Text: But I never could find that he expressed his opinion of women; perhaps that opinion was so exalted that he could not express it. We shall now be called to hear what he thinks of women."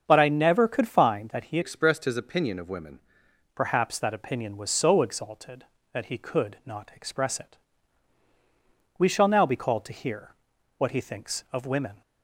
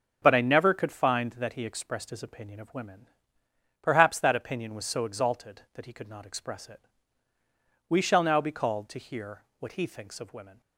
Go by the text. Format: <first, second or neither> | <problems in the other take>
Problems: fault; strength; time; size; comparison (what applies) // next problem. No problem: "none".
second | starts louder than the rest; until 1.0 s; 7 dB // changes voice from "expressed" to "women"; from 1.6 to 3.0 s; 1.4 s long // pauses between "hear" and "what"; at 10.3 s; 0.44 s long; slight in the second